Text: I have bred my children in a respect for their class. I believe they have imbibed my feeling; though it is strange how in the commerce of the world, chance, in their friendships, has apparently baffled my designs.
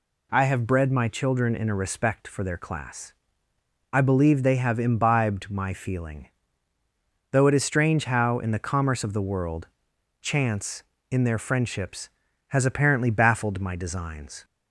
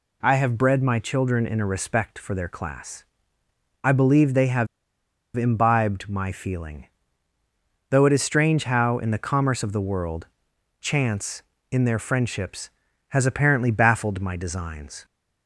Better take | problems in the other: first | pauses between "have" and "imbibed"; noticeable; at 4.6 s; 0.69 s long

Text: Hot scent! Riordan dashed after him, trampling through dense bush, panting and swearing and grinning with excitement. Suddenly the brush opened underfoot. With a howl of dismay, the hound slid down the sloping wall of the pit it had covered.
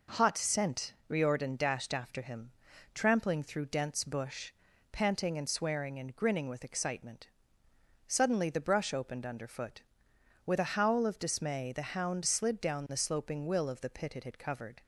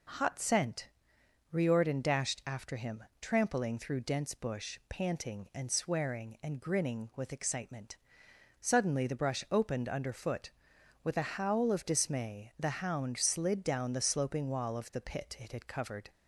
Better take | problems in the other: second | says "will" for "wall"; at 13.4 s

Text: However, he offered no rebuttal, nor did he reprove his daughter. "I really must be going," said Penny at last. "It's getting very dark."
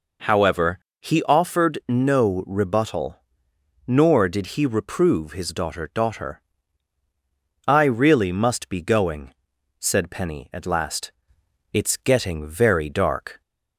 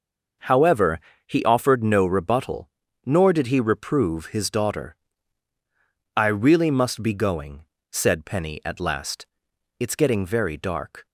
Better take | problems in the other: second | says "daughter" twice; at 5.9 s

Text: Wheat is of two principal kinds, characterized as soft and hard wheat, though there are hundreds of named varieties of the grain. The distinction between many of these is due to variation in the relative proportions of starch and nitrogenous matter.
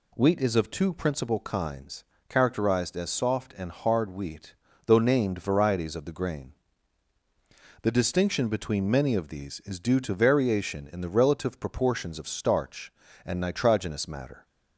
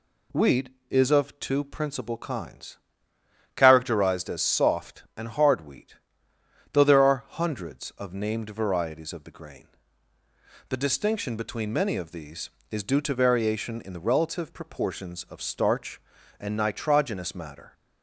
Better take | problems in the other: second | skips "there are hundreds of"; at 4.9 s

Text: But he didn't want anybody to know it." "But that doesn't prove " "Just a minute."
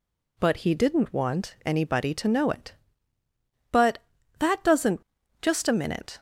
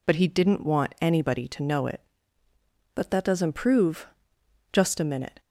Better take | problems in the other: second | skips "prove"; at 5.0 s

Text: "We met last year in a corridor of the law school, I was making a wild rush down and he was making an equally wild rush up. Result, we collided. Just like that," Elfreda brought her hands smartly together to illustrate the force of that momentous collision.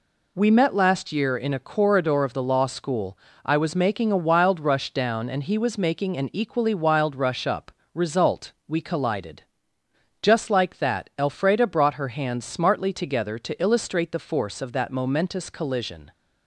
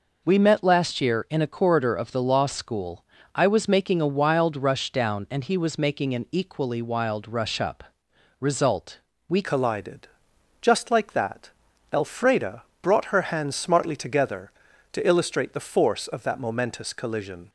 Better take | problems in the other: first | changes voice at "collided"; from 9.4 s on; 8.0 s long // pauses between "Elfreda" and "brought"; slight; at 12.6 s; 0.18 s long

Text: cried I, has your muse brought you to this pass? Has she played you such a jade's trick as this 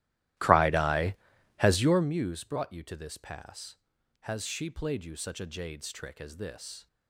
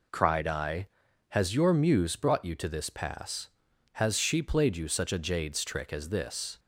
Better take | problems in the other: second | starts louder than the rest; strong; until 2.1 s; 15 dB

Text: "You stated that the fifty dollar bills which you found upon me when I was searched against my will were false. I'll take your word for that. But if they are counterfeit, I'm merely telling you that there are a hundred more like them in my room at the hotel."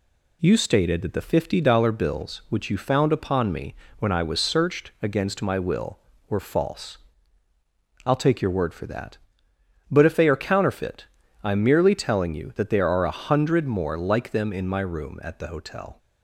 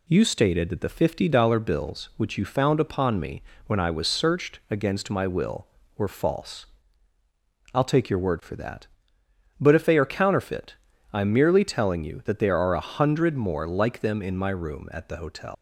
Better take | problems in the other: first | pauses between "me" and "when"; slight; at 3.4 s; 0.24 s long; slight in the first // leaves "hotel" unfinished; at 15.5 s; 120 ms

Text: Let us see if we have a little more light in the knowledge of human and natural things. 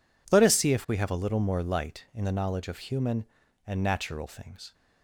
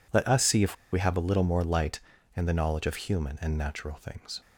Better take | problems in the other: first | pauses between "if" and "we"; slight; at 0.7 s; 0.19 s long

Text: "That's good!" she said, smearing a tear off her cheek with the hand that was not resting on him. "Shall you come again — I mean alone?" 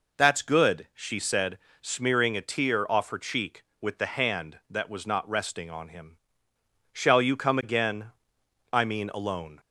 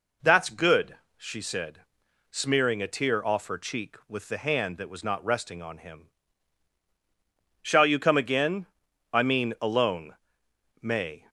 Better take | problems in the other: first | goes on to say "May"; slight; from 10.8 s on; 0.48 s long

